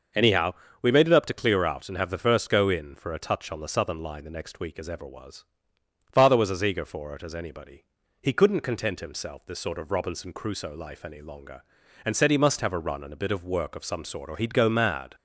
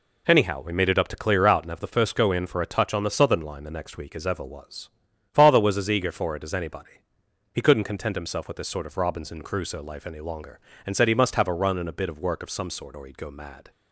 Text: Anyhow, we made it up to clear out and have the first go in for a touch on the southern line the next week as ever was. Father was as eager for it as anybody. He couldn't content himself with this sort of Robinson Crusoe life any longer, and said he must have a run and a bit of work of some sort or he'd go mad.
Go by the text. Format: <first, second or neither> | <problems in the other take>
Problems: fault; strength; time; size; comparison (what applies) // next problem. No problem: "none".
second | starts louder than the rest; noticeable; until 1.4 s; 6 dB // skips "with"; at 9.4 s